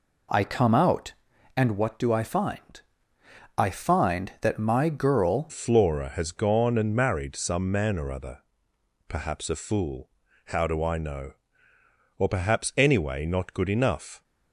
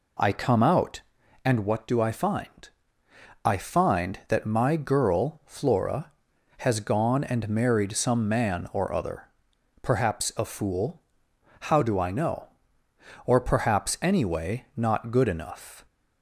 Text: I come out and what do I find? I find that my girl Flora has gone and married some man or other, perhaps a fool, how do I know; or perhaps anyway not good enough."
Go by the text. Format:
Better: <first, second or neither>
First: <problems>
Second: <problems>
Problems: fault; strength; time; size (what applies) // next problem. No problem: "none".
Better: second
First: changes voice at "Flora"; from 5.4 s on; 8.8 s long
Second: none